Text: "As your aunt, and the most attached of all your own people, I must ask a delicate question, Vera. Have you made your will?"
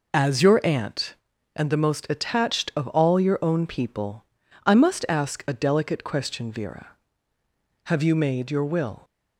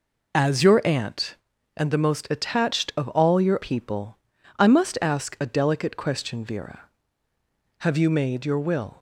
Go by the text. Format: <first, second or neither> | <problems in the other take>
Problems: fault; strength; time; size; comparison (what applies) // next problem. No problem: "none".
first | skips "own"; at 3.6 s